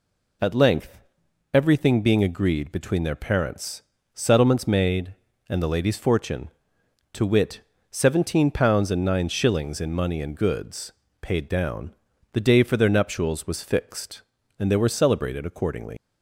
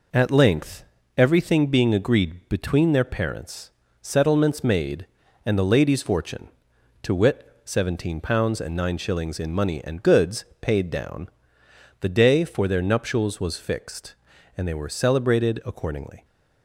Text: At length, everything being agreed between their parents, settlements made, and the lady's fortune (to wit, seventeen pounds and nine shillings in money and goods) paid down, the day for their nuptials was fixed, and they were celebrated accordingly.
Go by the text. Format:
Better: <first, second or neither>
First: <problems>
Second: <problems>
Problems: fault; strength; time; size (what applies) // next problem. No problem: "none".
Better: second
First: leaves "accordingly" unfinished; at 15.9 s; 85 ms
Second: none